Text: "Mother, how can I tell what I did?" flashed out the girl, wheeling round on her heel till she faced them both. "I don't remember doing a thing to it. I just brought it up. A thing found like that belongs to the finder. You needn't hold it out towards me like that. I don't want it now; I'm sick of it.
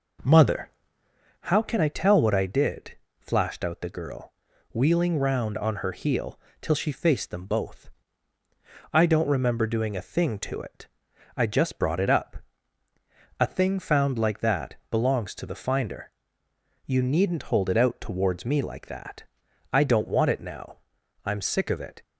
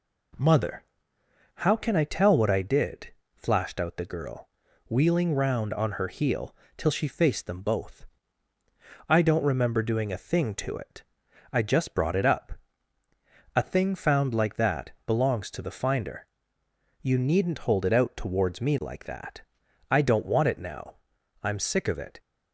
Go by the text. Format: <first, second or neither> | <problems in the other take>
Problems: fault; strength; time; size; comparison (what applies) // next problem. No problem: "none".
second | starts louder than the rest; noticeable; until 1.2 s; 5 dB // pauses between "heel" and "till"; slight; at 6.3 s; 0.20 s long; slight in the second // pauses between "that" and "belongs"; slight; at 14.7 s; 0.16 s long; slight in the second